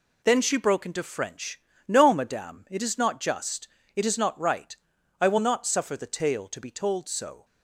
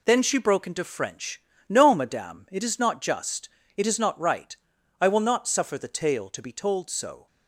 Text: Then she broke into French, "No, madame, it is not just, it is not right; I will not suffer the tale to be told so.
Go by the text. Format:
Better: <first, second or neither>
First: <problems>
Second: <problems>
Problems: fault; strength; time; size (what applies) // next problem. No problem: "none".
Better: neither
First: none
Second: none